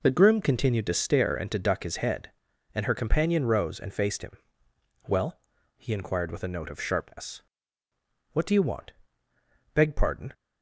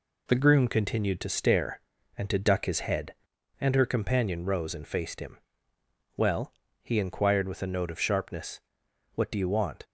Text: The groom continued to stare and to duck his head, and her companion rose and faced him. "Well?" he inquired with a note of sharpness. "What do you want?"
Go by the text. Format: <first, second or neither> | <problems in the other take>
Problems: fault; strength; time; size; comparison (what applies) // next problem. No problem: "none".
second | goes on to say "Beg pardon"; from 9.7 s on; 0.58 s long